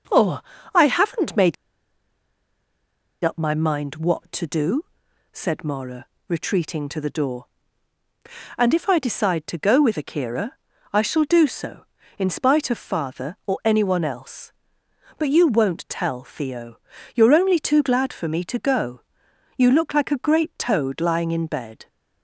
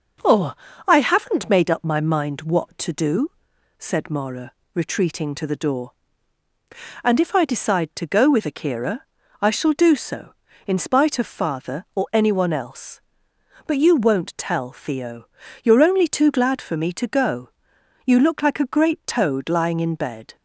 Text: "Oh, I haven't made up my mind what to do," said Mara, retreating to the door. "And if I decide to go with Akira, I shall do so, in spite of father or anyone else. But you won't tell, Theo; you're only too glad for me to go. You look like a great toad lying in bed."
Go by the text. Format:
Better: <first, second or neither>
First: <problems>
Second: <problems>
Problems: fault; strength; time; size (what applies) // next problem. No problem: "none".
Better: second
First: pauses between "made" and "up"; strong; at 1.5 s; 1.7 s long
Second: none